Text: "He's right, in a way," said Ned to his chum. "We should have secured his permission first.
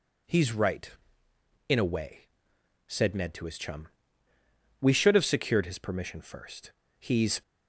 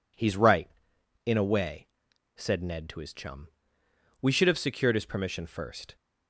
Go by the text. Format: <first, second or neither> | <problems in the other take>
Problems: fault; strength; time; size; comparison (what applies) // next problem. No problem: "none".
second | goes on to say "He's"; slight; from 6.9 s on; 0.42 s long